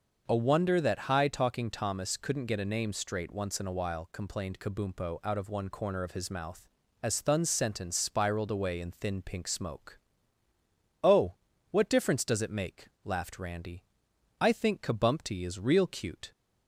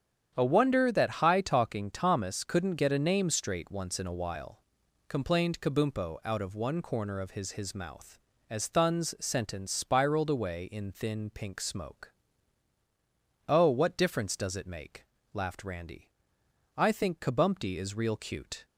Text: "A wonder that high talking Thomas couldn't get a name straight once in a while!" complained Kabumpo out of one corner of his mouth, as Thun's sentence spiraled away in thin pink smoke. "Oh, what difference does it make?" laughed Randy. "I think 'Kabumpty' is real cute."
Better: first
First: starts louder than the rest; until 1.2 s; 6 dB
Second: starts louder than the rest; strong; until 1.3 s; 8.5 dB // says "his" twice; at 7.5 s

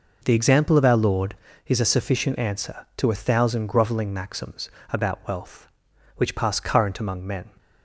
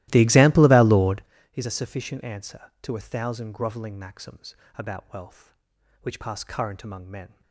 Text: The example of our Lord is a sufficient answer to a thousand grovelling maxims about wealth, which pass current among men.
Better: first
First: pauses between "maxims" and "about"; slight; at 4.6 s; 0.22 s long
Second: starts louder than the rest; strong; until 1.3 s; 16.5 dB // pauses between "maxims" and "about"; slight; at 4.5 s; 0.22 s long

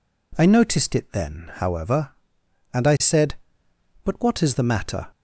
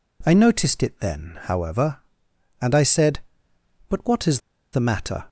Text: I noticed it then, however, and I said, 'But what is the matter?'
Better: first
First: none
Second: pauses between "is" and "the"; slight; at 4.3 s; 0.33 s long

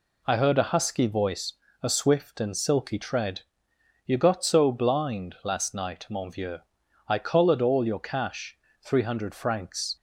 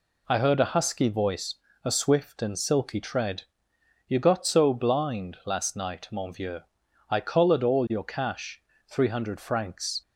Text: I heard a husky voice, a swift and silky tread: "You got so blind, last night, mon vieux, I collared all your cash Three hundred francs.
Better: neither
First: pauses between "cash" and "Three"; slight; at 8.5 s; 0.26 s long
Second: pauses between "cash" and "Three"; slight; at 8.6 s; 0.28 s long

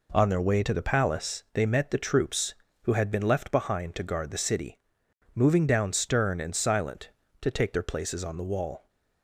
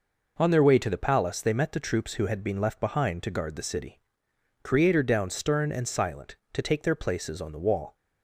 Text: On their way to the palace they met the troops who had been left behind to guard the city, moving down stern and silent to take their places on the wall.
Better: first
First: none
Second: says "creator" for "moving"; at 4.6 s

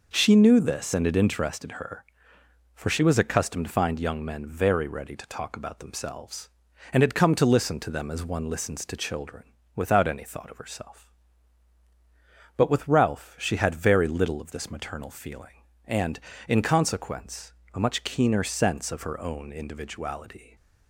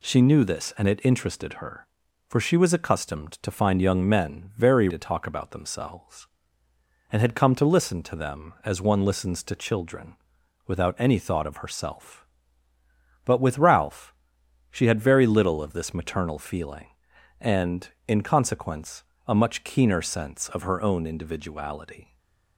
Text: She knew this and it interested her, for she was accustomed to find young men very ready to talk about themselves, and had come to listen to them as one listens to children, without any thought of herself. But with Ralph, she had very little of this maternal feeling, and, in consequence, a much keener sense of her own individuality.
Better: first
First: none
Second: skips "ready"; at 4.8 s // stays silent after the last word; slight; from 22.0 s on; 0.5 s long

